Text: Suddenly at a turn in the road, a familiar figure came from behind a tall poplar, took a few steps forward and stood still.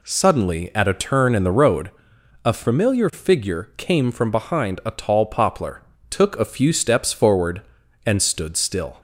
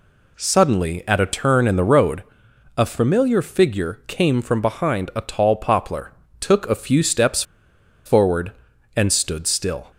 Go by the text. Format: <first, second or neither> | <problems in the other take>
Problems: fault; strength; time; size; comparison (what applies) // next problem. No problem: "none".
first | pauses between "steps" and "forward"; noticeable; at 7.4 s; 0.63 s long